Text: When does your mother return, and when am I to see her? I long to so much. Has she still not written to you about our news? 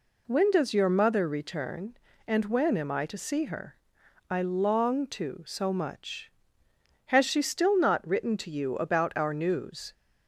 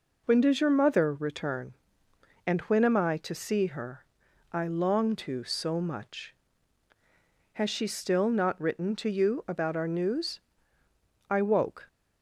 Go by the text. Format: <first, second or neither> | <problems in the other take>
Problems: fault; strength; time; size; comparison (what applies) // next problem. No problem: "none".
first | goes on to say "I woke"; from 11.2 s on; 0.58 s long